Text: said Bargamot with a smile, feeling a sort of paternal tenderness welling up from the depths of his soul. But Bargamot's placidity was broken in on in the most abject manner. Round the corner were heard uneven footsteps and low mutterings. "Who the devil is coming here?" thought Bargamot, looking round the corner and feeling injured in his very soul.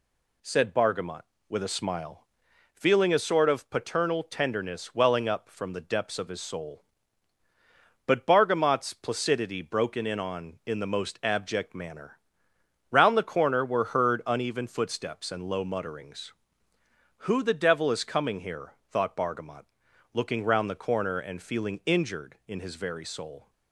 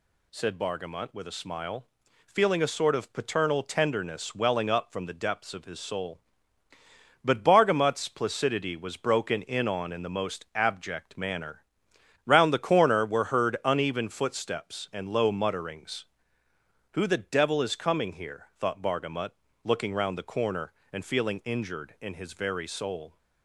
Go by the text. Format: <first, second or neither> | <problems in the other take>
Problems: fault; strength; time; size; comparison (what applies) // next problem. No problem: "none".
second | skips "was"; at 9.6 s